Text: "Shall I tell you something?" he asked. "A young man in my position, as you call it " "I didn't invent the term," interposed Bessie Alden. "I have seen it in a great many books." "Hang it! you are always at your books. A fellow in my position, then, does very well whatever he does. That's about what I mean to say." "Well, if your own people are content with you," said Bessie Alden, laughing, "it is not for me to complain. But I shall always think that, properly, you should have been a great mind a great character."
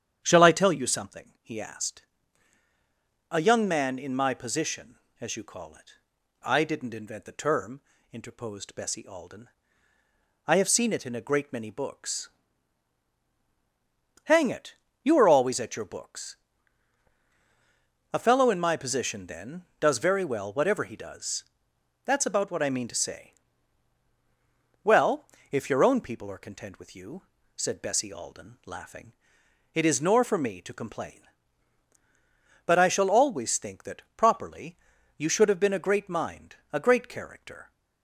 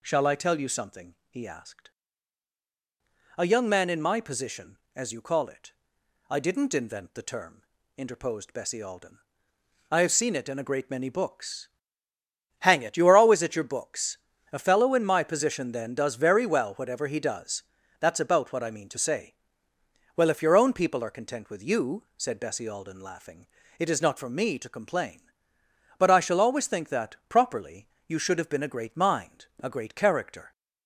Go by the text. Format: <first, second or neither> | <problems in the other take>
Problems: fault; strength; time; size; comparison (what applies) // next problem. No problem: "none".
second | starts louder than the rest; strong; until 1.2 s; 9.5 dB // says "nor" for "not"; at 29.9 s // pauses between "mind" and "a"; slight; at 36.5 s; 0.16 s long